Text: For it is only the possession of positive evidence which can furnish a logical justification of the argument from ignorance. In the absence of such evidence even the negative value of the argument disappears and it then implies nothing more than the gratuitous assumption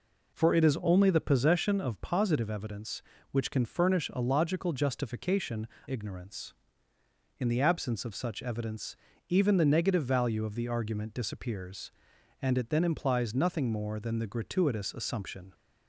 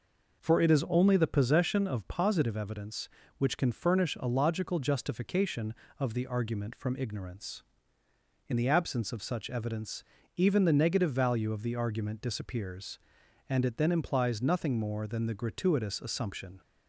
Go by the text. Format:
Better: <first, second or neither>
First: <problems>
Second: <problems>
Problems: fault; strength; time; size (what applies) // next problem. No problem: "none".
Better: second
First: skips "of the argument from"; at 5.7 s // pauses between "evidence" and "even"; slight; at 8.9 s; 0.32 s long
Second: pauses between "evidence" and "even"; slight; at 10.0 s; 0.32 s long